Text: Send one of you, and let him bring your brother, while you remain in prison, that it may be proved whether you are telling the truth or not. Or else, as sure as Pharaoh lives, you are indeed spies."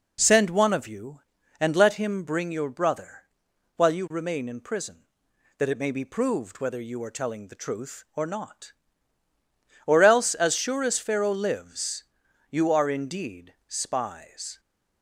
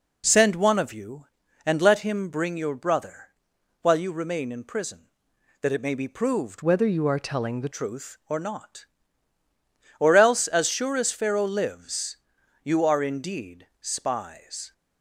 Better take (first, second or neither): first